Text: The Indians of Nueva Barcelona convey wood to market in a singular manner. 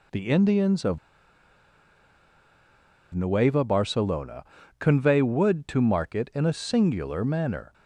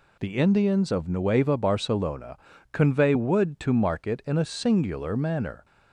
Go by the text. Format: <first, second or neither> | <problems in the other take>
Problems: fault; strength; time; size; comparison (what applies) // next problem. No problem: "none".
second | pauses between "of" and "Nueva"; strong; at 0.9 s; 2.1 s long // pauses between "Barcelona" and "convey"; slight; at 4.4 s; 0.36 s long; slight in the second